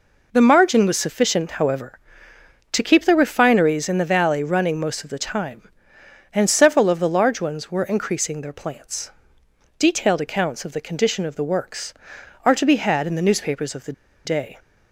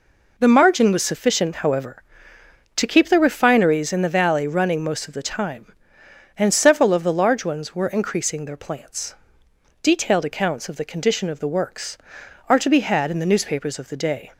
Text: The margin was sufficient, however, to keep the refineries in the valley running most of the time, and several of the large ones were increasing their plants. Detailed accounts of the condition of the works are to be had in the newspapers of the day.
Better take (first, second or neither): second